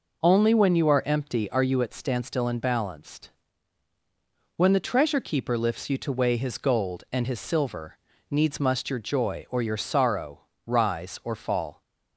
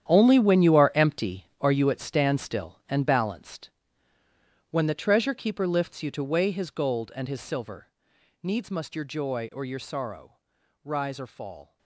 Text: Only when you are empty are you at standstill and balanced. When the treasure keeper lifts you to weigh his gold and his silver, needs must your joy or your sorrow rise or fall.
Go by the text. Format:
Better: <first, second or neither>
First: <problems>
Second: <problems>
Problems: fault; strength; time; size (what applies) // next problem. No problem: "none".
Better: first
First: pauses between "sorrow" and "rise"; slight; at 10.4 s; 0.24 s long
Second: gets quieter; strong; throughout; 13.5 dB // pauses between "sorrow" and "rise"; at 10.3 s; 0.44 s long